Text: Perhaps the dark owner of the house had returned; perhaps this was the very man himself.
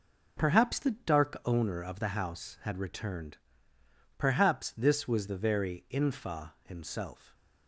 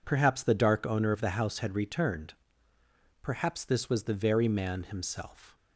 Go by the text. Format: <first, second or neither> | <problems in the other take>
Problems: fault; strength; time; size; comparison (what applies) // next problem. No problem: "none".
second | says "infa" for "man"; at 5.8 s